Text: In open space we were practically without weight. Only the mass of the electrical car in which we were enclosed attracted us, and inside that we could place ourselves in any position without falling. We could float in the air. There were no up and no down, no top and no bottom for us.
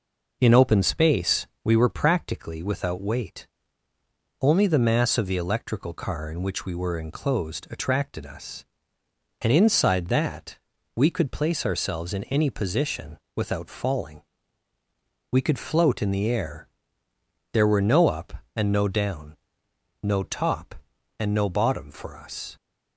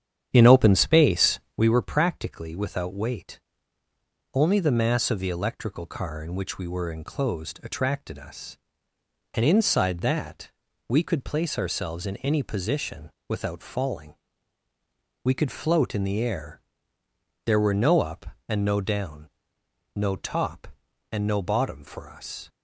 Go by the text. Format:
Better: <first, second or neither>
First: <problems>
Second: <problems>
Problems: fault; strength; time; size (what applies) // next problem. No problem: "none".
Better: first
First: pauses between "space" and "we"; slight; at 1.4 s; 0.18 s long // pauses between "that" and "we"; at 10.5 s; 0.38 s long // pauses between "position" and "without"; slight; at 13.1 s; 0.18 s long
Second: starts louder than the rest; strong; until 1.7 s; 9 dB // pauses between "space" and "we"; slight; at 1.4 s; 0.18 s long // pauses between "that" and "we"; at 10.5 s; 0.38 s long // pauses between "position" and "without"; slight; at 13.1 s; 0.18 s long